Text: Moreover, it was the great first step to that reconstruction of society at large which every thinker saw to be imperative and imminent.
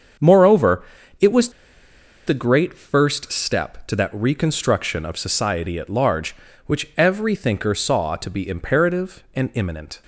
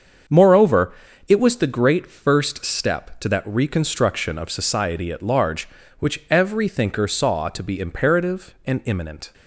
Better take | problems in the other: second | starts louder than the rest; until 2.3 s; 7 dB; also in the second // pauses between "was" and "the"; noticeable; at 1.4 s; 0.77 s long

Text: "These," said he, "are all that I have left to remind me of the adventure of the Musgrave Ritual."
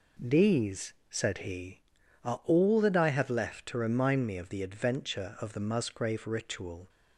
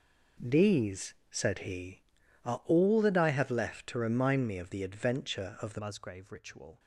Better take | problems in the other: first | changes voice at "Musgrave"; from 5.7 s on; 1.0 s long

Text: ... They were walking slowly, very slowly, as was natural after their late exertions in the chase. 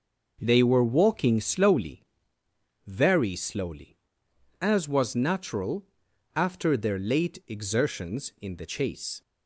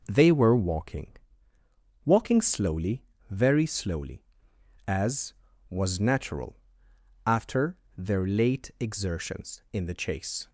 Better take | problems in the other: first | says "walking" twice; at 2.0 s // pauses between "natural" and "after"; noticeable; at 6.5 s; 0.68 s long; noticeable in the first // pauses between "after" and "their"; slight; at 7.7 s; 0.20 s long

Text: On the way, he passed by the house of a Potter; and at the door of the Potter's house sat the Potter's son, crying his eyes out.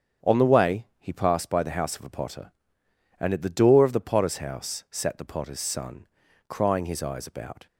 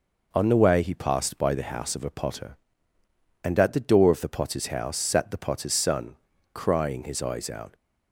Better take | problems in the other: second | starts louder than the rest; strong; until 1.3 s; 7.5 dB // says "about" for "out"; at 7.2 s

